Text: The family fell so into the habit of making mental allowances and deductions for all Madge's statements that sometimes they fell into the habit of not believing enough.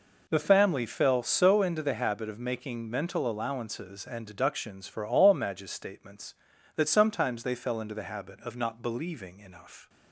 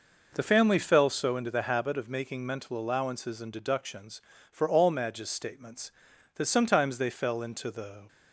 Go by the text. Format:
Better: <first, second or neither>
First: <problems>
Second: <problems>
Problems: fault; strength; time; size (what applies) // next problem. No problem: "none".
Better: first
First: none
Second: stops before "habit of not believing enough"; at 8.0 s